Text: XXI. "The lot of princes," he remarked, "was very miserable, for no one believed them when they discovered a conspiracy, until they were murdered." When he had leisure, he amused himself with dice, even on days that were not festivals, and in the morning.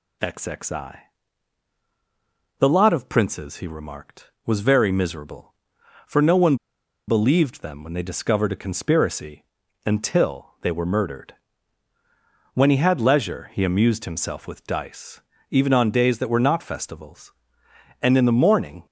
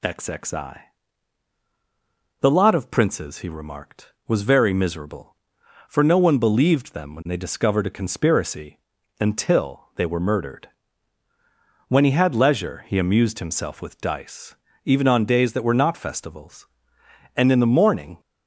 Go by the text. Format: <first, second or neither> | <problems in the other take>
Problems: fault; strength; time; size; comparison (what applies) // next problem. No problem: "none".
second | pauses between "one" and "believed"; noticeable; at 6.5 s; 0.52 s long